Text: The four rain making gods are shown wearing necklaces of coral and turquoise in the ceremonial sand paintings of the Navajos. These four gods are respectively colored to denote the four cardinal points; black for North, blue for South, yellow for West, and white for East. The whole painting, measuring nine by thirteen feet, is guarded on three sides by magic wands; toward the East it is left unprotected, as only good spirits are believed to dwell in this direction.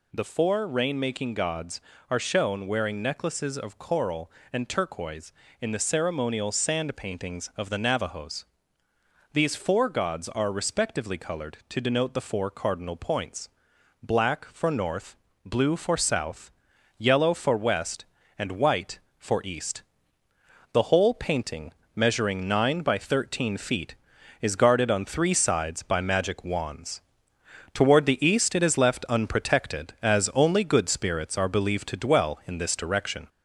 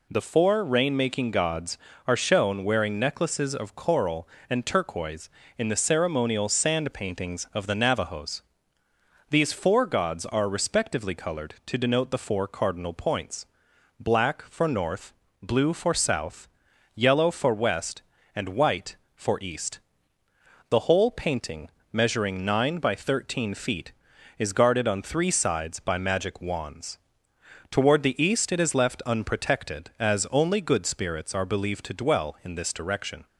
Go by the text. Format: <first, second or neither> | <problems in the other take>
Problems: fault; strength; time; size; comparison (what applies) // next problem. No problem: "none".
second | gets louder; slight; throughout; 2.5 dB